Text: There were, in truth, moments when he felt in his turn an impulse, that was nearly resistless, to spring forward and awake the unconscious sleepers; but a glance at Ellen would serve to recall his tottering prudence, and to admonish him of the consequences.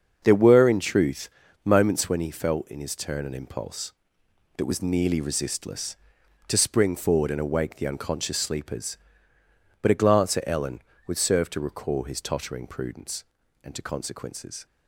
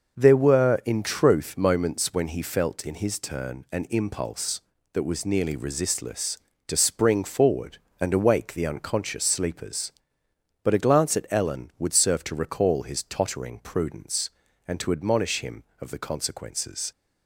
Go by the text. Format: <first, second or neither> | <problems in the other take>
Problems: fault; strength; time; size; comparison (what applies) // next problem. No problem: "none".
second | starts louder than the rest; until 1.2 s; 6.5 dB; noticeable in the second // skips "admonish him of the"; at 13.8 s